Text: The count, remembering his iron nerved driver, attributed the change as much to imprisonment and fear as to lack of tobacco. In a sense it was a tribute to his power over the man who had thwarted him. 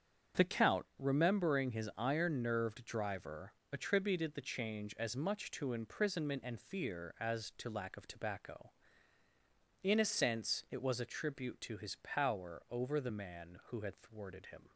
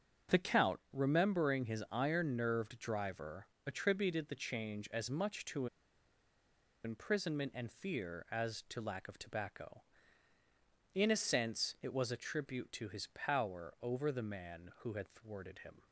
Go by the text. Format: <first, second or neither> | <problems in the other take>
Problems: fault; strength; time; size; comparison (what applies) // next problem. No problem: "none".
first | starts louder than the rest; until 1.4 s; 7 dB; also in the first // pauses between "to" and "imprisonment"; at 5.6 s; 1.1 s long